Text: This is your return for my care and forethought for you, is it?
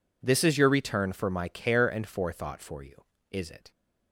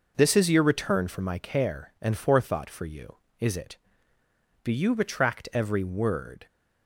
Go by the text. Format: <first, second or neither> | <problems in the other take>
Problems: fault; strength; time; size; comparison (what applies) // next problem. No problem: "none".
first | goes on to say "Do you retract every word"; strong; from 4.6 s on; 1.8 s long